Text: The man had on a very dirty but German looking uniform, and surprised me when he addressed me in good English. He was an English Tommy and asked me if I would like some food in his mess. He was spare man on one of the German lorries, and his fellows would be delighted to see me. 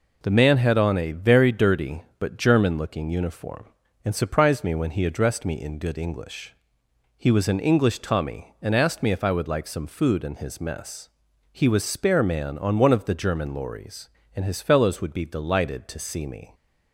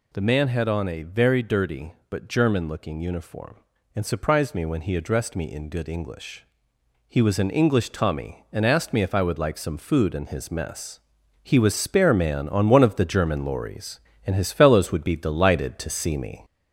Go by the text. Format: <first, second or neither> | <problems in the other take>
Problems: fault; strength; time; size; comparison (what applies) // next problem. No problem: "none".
first | gets louder; slight; throughout; 3 dB